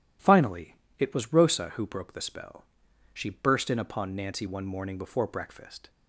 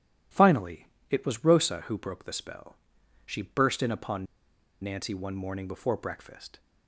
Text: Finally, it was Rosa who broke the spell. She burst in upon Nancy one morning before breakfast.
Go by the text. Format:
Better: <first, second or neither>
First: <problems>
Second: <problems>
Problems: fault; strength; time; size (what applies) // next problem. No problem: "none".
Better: first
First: none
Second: pauses between "upon" and "Nancy"; noticeable; at 4.2 s; 0.57 s long